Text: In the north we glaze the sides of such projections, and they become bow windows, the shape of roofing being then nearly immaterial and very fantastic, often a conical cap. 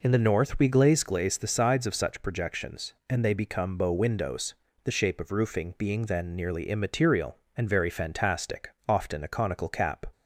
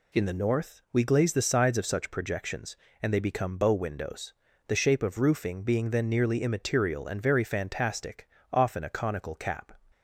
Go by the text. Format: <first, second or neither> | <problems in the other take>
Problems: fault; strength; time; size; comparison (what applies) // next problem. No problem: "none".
second | says "glaze" twice; at 1.0 s